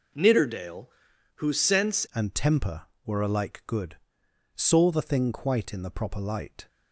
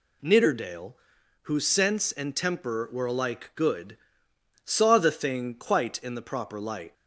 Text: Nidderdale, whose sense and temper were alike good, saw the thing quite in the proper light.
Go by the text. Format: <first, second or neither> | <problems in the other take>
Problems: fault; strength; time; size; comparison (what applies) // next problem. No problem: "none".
second | changes voice at "and"; from 2.1 s on; 4.5 s long